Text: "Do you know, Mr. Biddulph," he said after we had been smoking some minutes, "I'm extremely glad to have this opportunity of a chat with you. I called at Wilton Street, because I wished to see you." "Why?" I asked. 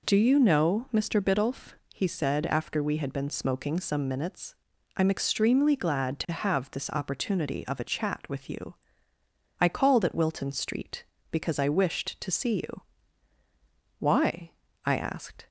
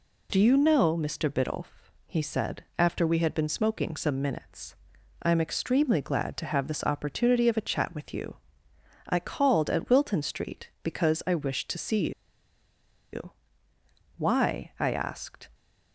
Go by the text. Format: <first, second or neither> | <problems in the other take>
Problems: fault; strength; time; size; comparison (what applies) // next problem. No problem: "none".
first | pauses between "said" and "after"; slight; at 2.6 s; 0.16 s long // pauses between "see" and "you"; at 12.0 s; 1.0 s long